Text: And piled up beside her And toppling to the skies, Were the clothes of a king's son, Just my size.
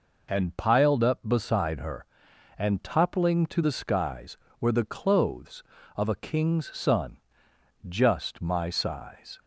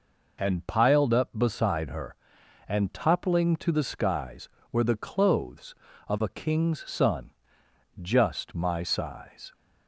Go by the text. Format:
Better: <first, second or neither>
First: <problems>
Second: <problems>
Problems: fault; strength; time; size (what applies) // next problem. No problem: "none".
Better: neither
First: none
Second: none